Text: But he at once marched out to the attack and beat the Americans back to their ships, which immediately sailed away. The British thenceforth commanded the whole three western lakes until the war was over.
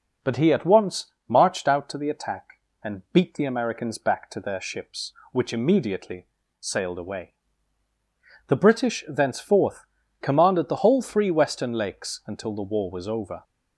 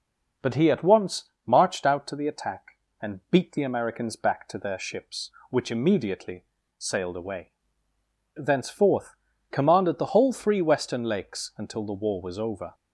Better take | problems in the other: first | pauses between "once" and "marched"; slight; at 1.3 s; 0.16 s long; slight in the first // pauses between "immediately" and "sailed"; slight; at 6.4 s; 0.32 s long; slight in the first // skips "The British"; at 7.9 s // pauses between "thenceforth" and "commanded"; slight; at 9.1 s; 0.36 s long; slight in the first

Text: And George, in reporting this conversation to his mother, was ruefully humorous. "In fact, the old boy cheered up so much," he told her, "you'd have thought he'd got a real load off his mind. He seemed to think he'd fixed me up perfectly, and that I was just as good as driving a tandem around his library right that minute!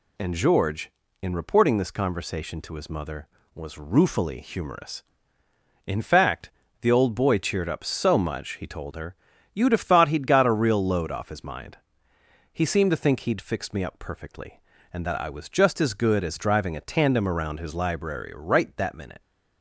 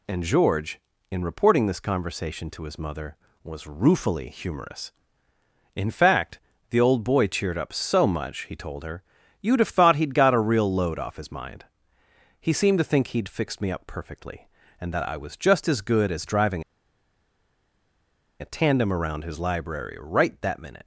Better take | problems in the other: first | pauses between "driving" and "a"; strong; at 16.6 s; 1.7 s long

